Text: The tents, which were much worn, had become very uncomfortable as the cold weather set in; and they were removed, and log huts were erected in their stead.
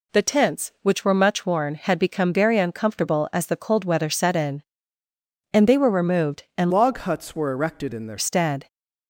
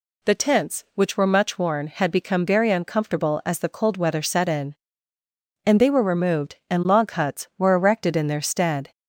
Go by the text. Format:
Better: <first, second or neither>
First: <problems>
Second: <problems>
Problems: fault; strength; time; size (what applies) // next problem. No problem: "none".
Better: second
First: changes voice from "log" to "their"; from 6.7 to 8.1 s; 1.4 s long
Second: none